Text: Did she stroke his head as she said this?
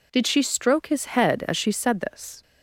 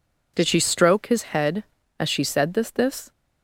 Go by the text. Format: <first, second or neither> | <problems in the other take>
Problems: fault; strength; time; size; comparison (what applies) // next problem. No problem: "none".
first | says "this" twice; at 2.7 s